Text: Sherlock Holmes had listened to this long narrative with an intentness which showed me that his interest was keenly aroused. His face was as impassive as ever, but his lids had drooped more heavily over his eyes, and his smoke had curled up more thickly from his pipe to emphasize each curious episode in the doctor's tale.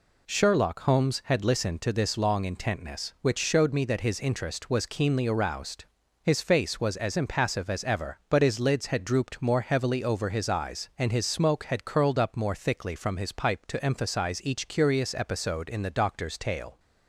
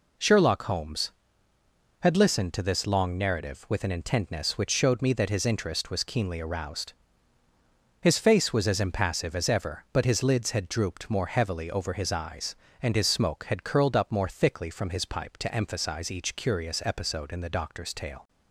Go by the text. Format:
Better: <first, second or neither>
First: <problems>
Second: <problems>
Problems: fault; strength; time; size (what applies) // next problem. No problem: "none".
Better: second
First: skips "narrative with an"; at 2.4 s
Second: none